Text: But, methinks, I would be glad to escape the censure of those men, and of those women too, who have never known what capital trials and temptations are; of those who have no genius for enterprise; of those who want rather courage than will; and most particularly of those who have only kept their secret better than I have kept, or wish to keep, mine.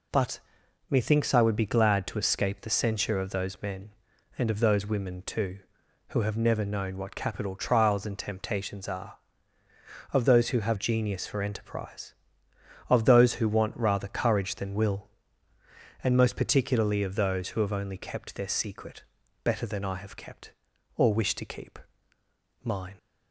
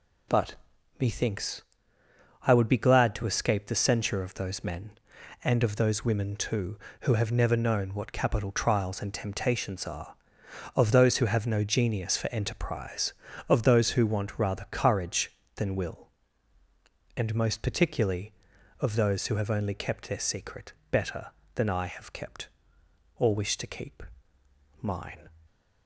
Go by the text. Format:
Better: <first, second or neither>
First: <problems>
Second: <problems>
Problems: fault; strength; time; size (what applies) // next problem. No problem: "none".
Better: second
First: skips "no"; at 10.7 s // pauses between "secret" and "better"; at 19.0 s; 0.40 s long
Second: pauses between "secret" and "better"; slight; at 20.7 s; 0.16 s long